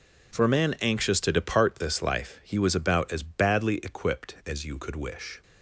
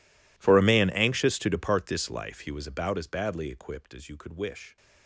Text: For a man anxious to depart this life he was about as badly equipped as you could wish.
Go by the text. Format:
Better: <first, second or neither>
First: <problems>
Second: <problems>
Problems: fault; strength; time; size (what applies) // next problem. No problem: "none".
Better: first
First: none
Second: gets quieter; strong; throughout; 24 dB